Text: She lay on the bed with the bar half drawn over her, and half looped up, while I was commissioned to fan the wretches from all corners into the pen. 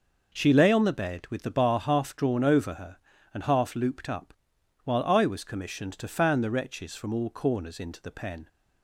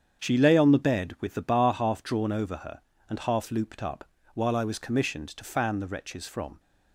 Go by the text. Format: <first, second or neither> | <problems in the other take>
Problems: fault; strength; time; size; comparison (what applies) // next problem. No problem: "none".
first | starts louder than the rest; strong; until 1.2 s; 7.5 dB // stops before "all corners into the pen"; at 6.5 s